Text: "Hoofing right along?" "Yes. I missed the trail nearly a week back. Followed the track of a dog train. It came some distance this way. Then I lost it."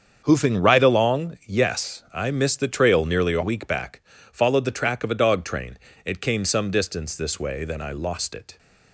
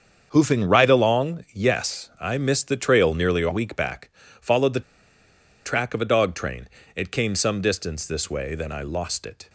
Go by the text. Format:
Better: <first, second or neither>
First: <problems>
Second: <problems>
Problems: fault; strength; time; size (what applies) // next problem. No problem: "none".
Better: first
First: starts louder than the rest; strong; until 1.2 s; 7.5 dB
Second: starts louder than the rest; strong; until 1.3 s; 7.5 dB // pauses between "the" and "track"; noticeable; at 4.8 s; 0.83 s long